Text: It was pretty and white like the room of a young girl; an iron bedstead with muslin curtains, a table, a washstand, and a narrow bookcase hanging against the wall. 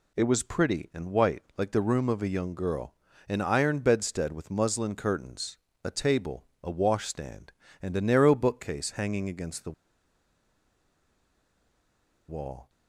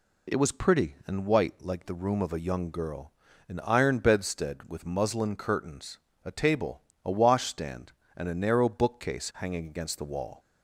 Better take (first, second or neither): second